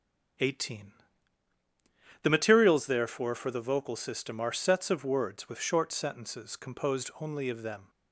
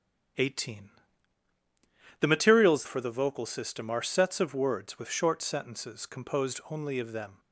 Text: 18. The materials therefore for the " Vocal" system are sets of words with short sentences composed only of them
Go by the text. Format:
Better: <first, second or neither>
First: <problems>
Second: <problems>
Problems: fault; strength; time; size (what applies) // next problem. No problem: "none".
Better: first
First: starts louder than the rest; strong; until 2.6 s; 7.5 dB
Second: starts louder than the rest; strong; until 2.6 s; 9 dB // skips "therefore"; at 2.8 s